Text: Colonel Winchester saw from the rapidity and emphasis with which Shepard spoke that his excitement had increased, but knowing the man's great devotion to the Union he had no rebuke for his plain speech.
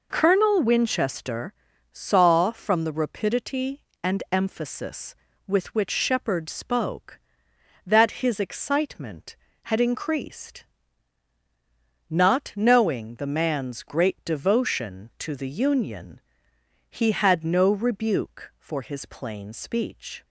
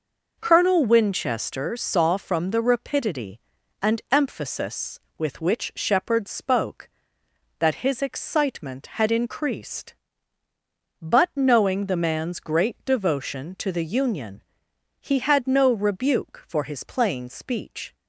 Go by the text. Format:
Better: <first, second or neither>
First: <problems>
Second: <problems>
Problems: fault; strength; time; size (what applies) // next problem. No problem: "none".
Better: second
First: pauses between "Winchester" and "saw"; at 1.5 s; 0.40 s long // says "not" for "but"; at 12.0 s // pauses between "Union" and "he"; noticeable; at 16.1 s; 0.70 s long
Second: pauses between "Union" and "he"; noticeable; at 14.4 s; 0.58 s long